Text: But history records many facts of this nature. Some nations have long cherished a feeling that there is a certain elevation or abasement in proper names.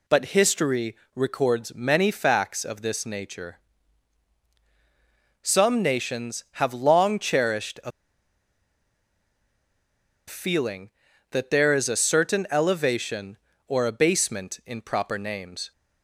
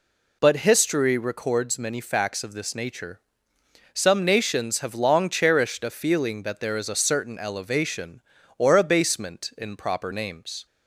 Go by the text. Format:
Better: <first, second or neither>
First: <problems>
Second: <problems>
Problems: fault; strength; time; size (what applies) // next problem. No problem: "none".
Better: second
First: pauses between "history" and "records"; slight; at 0.9 s; 0.20 s long // pauses between "a" and "feeling"; strong; at 7.9 s; 2.3 s long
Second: none